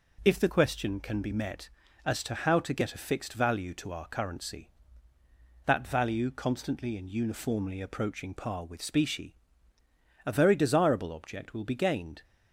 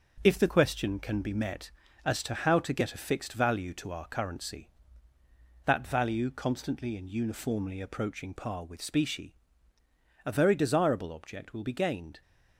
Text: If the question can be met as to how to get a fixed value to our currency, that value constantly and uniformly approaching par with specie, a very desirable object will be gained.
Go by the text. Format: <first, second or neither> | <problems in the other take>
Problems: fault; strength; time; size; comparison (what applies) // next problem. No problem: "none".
first | gets quieter; noticeable; throughout; 5.5 dB